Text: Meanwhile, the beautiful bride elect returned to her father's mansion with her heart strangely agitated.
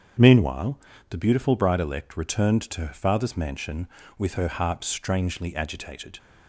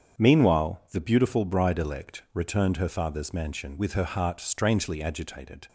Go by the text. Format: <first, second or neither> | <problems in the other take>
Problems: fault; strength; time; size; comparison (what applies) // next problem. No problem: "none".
first | starts louder than the rest; strong; until 1.3 s; 7.5 dB; strong in the first // skips "to"; at 2.7 s